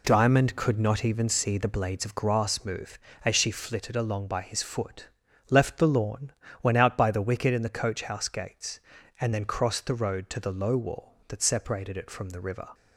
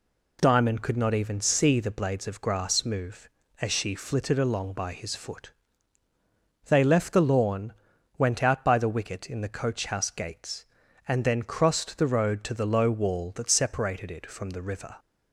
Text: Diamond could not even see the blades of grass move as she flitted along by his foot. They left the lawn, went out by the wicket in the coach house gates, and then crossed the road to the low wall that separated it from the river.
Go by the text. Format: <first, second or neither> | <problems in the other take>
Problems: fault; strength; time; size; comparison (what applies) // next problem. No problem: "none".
second | skips "They"; at 5.2 s